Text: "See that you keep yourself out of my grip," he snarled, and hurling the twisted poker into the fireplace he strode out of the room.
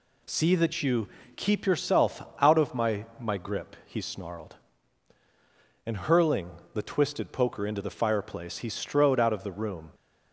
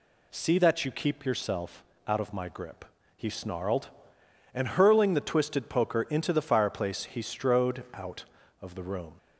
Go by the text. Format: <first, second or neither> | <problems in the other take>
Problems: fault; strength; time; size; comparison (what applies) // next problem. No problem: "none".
second | pauses between "you" and "keep"; slight; at 1.0 s; 0.28 s long // pauses between "yourself" and "out"; slight; at 2.2 s; 0.18 s long; slight in the second // says "my" twice; at 3.1 s // pauses between "hurling" and "the"; slight; at 6.5 s; 0.22 s long